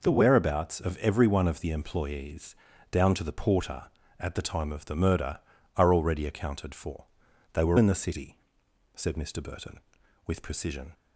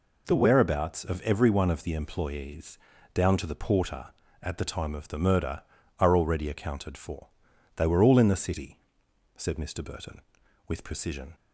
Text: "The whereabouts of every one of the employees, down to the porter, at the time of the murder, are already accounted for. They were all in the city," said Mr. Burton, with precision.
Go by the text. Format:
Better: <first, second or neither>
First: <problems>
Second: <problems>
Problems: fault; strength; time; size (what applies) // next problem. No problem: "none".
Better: second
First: skips "all"; at 7.7 s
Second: none